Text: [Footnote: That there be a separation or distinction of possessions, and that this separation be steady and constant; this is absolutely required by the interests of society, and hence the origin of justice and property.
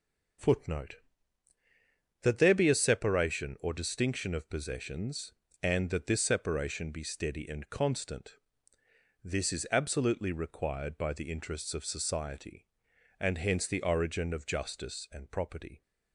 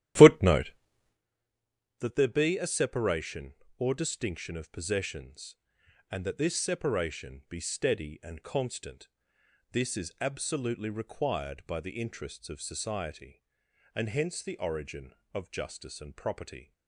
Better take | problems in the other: first | starts louder than the rest; strong; until 1.2 s; 11 dB

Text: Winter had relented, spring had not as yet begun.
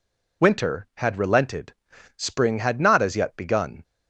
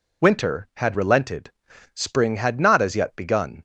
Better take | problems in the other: neither | none

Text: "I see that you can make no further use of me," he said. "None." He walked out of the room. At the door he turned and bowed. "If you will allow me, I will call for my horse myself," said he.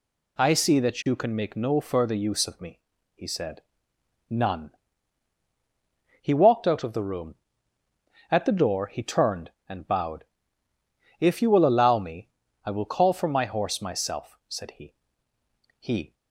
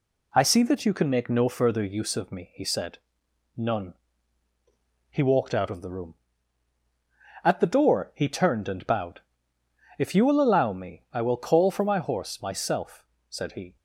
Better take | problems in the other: second | goes on to say "He"; slight; from 15.7 s on; 0.34 s long

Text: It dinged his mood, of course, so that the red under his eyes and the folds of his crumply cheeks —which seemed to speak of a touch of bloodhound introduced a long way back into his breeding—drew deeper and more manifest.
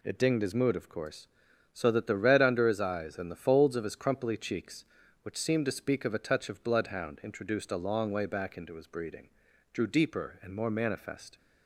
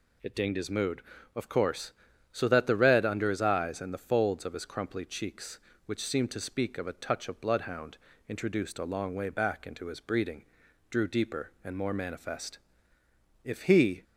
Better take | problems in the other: first | pauses between "bloodhound" and "introduced"; slight; at 7.9 s; 0.30 s long // goes on to say "If he"; from 13.4 s on; 0.60 s long

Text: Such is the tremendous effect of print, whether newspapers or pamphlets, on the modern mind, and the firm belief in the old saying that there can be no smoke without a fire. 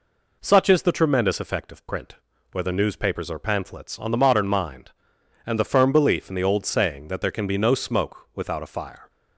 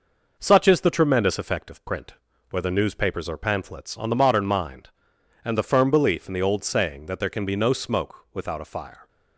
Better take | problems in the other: first | gets quieter; noticeable; throughout; 4.5 dB

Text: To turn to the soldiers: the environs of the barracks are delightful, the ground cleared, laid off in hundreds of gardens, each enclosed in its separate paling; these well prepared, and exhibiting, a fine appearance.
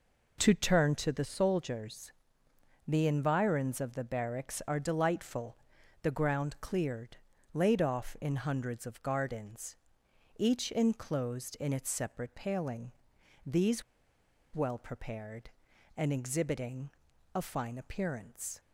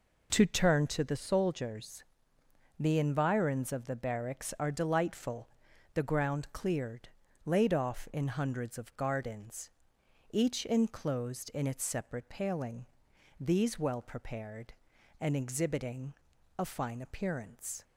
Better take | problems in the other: second | pauses between "these" and "well"; noticeable; at 13.8 s; 0.71 s long

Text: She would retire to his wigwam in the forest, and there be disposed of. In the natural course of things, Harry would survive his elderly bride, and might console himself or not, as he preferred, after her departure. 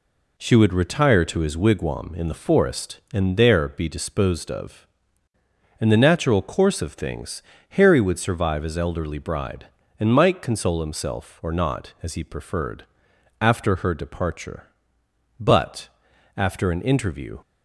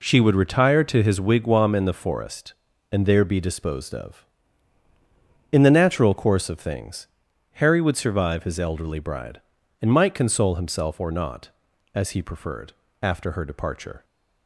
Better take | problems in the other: second | goes on to say "But after an interview"; strong; from 15.3 s on; 2.0 s long

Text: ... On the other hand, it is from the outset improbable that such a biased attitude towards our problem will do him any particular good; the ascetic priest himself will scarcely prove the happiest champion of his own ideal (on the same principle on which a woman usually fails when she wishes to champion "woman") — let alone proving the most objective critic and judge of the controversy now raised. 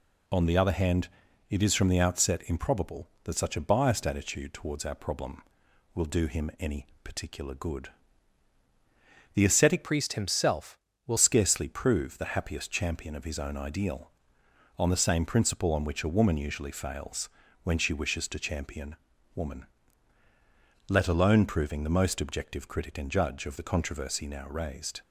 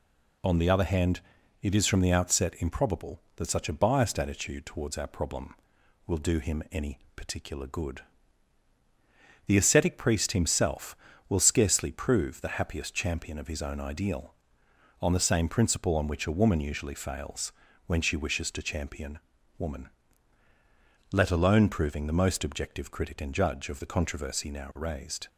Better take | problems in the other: second | pauses between "any" and "particular"; slight; at 6.8 s; 0.16 s long; slight in the second // changes voice from "priest" to "will"; from 9.8 to 11.1 s; 1.3 s long // pauses between "fails" and "when"; slight; at 17.2 s; 0.36 s long; slight in the second // pauses between "champion" and "woman"; at 18.9 s; 0.40 s long; also in the second

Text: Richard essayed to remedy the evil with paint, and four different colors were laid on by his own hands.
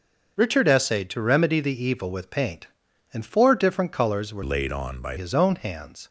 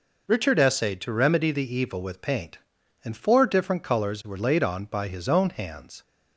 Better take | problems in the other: second | starts louder than the rest; until 1.3 s; 6 dB // changes voice from "laid" to "by"; from 4.4 to 5.1 s; 0.7 s long

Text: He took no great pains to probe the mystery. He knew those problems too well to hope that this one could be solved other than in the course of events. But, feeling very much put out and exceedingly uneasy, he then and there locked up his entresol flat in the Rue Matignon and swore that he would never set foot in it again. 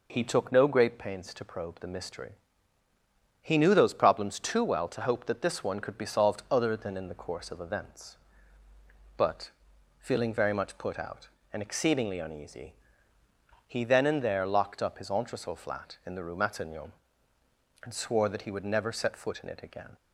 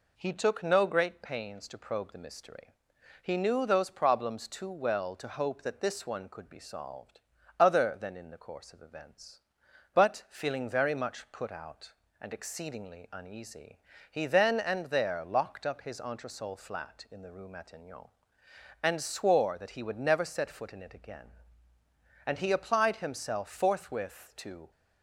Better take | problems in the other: first | pauses between "solved" and "other"; at 7.2 s; 0.38 s long // goes on to say "And he applied himself forthwith to"; strong; from 22.2 s on; 2.4 s long

